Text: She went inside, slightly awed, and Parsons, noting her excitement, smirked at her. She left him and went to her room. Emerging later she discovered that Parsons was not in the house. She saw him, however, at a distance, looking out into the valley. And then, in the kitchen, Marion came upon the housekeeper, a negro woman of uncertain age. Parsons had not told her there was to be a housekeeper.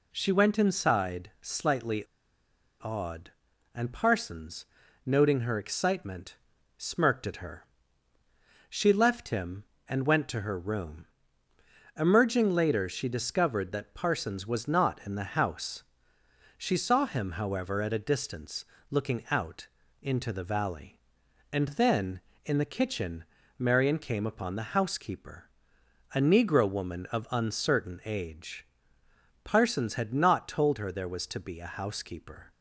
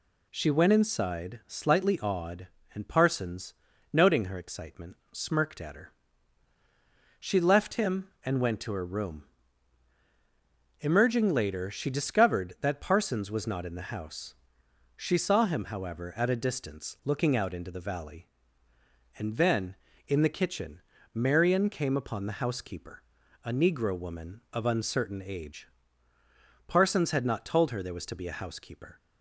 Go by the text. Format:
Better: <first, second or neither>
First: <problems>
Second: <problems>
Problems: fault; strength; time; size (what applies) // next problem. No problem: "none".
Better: second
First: pauses between "slightly" and "awed"; noticeable; at 2.0 s; 0.75 s long // pauses between "out" and "into"; slight; at 19.6 s; 0.36 s long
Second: none